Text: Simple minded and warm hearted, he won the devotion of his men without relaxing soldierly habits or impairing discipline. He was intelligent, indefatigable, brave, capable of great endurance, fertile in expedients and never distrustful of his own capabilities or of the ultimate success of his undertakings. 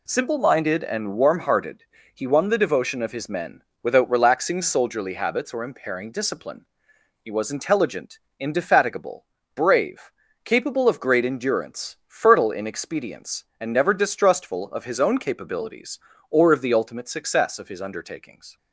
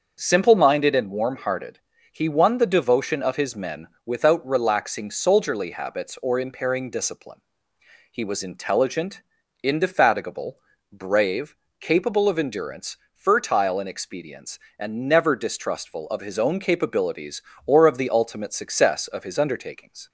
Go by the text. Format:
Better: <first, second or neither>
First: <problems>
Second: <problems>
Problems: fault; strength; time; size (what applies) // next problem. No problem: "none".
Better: first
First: pauses between "men" and "without"; slight; at 3.6 s; 0.22 s long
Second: starts louder than the rest; until 1.2 s; 6.5 dB // pauses between "men" and "without"; slight; at 3.8 s; 0.18 s long // skips "great"; at 12.3 s